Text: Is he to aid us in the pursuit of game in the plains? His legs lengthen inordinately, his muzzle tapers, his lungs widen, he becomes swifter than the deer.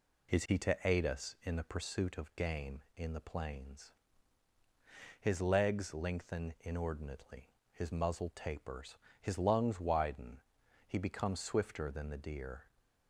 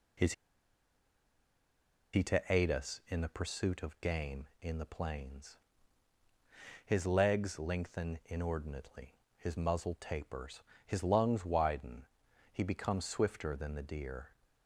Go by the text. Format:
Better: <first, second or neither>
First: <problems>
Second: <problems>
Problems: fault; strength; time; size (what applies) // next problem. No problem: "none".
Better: first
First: none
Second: pauses between "Is" and "he"; strong; at 0.3 s; 1.8 s long